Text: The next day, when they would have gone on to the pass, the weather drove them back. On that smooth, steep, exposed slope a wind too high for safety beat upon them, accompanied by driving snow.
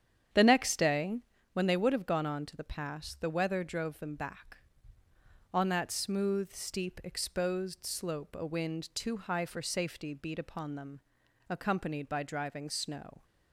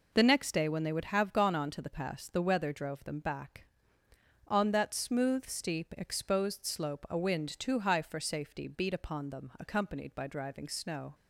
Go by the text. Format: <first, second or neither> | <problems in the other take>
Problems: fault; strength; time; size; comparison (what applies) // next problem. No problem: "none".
second | starts louder than the rest; strong; until 1.4 s; 9 dB